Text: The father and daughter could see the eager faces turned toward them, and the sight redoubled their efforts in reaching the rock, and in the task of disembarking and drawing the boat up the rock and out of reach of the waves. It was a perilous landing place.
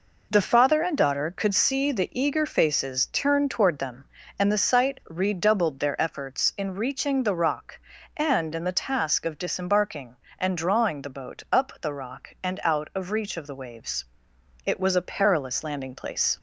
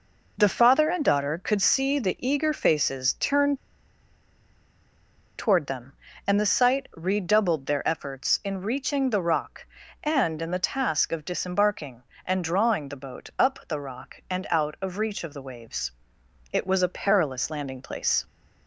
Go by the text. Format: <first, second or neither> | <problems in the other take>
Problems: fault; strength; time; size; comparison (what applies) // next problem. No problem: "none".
first | pauses between "turned" and "toward"; strong; at 3.5 s; 1.8 s long